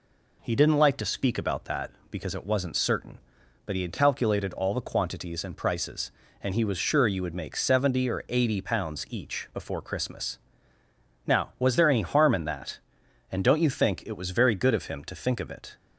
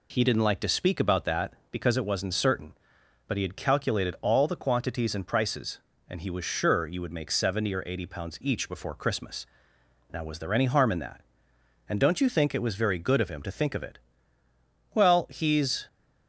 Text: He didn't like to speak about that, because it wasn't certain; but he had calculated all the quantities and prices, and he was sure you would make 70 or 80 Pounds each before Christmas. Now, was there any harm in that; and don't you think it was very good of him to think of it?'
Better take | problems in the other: first | goes on to say "Well he's"; noticeable; from 14.9 s on; 0.94 s long

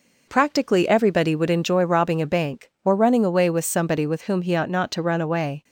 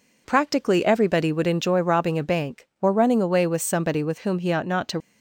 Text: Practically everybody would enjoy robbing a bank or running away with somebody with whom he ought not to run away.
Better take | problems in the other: first | stops before "run away"; at 4.9 s

